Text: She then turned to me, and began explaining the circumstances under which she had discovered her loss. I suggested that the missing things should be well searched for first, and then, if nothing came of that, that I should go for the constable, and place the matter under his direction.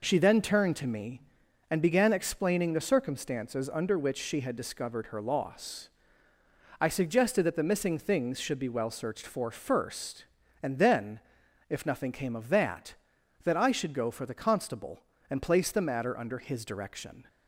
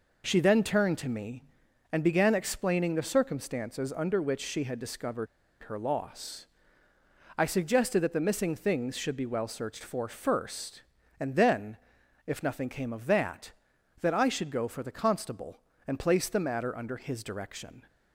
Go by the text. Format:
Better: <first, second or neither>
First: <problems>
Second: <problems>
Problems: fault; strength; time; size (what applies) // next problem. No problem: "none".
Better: first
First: none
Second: pauses between "discovered" and "her"; at 5.2 s; 0.36 s long